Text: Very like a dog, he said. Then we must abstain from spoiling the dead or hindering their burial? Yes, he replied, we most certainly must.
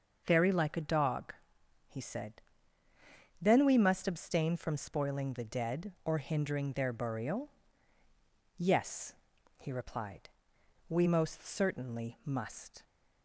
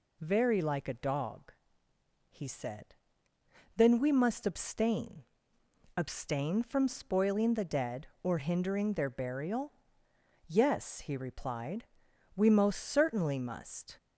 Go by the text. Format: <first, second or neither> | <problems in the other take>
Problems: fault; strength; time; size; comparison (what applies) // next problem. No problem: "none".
first | says "abstain" twice; at 5.9 s